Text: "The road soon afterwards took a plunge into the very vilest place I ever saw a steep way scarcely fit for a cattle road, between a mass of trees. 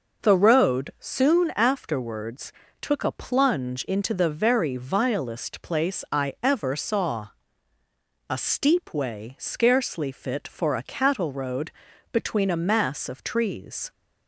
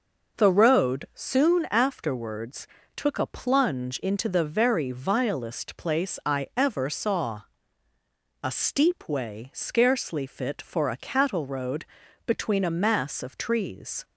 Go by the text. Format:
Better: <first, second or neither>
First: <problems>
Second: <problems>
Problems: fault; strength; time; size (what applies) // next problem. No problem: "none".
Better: neither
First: pauses between "afterwards" and "took"; slight; at 2.5 s; 0.30 s long // pauses between "saw" and "a"; noticeable; at 7.2 s; 0.98 s long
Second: pauses between "afterwards" and "took"; slight; at 2.6 s; 0.30 s long // pauses between "saw" and "a"; noticeable; at 7.4 s; 0.98 s long